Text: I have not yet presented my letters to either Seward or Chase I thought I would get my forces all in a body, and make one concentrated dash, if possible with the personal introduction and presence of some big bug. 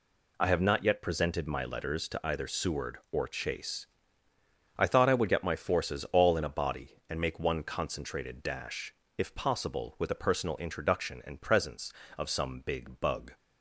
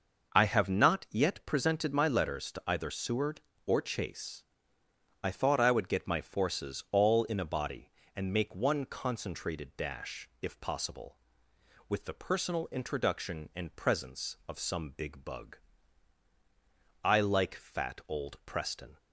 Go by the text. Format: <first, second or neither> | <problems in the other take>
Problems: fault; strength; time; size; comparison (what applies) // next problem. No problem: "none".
first | pauses between "Chase" and "I"; noticeable; at 4.4 s; 0.80 s long; noticeable in the first // goes on to say "I like fat old Preston"; strong; from 17.0 s on; 1.9 s long